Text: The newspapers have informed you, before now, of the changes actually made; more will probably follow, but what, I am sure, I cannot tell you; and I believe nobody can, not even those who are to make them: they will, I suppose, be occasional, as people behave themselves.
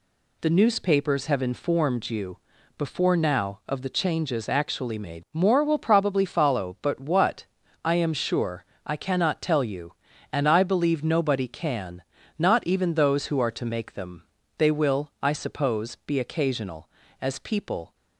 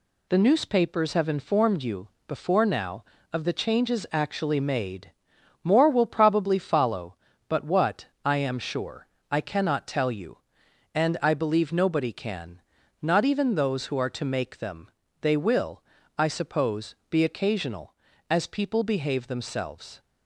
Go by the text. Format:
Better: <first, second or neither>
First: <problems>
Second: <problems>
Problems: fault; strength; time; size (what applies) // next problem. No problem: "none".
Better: second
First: stops before "behave themselves"; at 17.9 s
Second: none